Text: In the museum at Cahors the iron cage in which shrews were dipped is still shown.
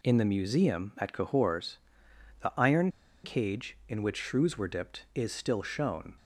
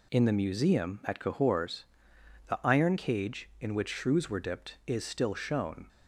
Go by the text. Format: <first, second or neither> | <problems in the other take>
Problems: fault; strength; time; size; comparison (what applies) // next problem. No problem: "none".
second | pauses between "Cahors" and "the"; noticeable; at 1.7 s; 0.64 s long; noticeable in the second // pauses between "iron" and "cage"; slight; at 2.8 s; 0.34 s long